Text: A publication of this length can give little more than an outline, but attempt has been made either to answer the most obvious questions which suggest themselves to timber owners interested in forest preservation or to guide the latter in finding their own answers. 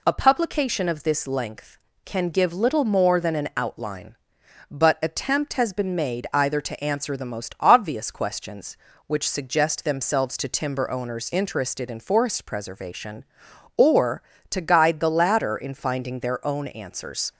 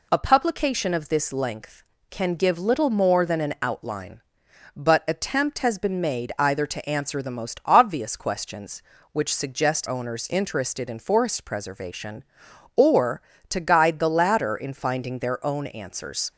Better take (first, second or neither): first